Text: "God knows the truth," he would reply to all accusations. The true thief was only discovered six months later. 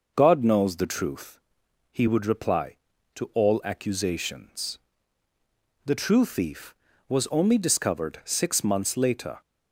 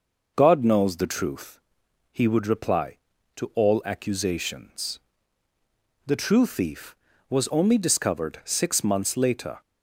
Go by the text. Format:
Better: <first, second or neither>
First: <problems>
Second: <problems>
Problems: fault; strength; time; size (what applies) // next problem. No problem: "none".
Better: neither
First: none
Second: none